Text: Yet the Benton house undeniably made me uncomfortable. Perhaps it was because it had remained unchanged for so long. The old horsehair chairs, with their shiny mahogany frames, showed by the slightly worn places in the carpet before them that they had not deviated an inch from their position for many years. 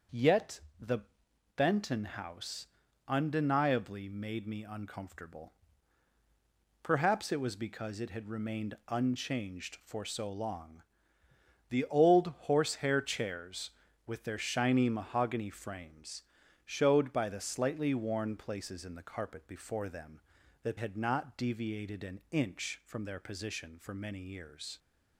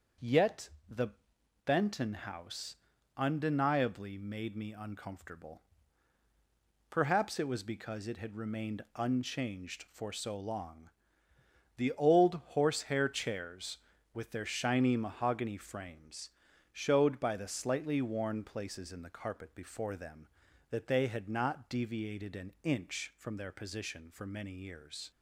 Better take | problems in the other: second | starts louder than the rest; until 1.8 s; 6.5 dB; also in the second // pauses between "Yet" and "the"; slight; at 0.6 s; 0.18 s long; slight in the second // pauses between "the" and "Benton"; noticeable; at 0.9 s; 0.56 s long; noticeable in the second // pauses between "house" and "undeniably"; at 2.6 s; 0.42 s long; also in the second // skips "they"; at 20.7 s

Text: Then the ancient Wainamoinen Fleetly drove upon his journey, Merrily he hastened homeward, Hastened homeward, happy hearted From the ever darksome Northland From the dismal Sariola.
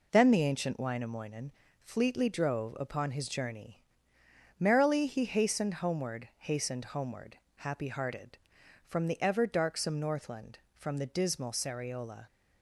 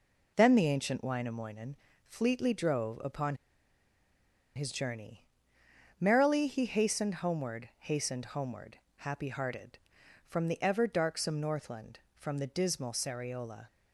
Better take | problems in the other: first | pauses between "Wainamoinen" and "Fleetly"; slight; at 1.7 s; 0.32 s long; slight in the first // pauses between "upon" and "his"; at 3.3 s; 1.2 s long

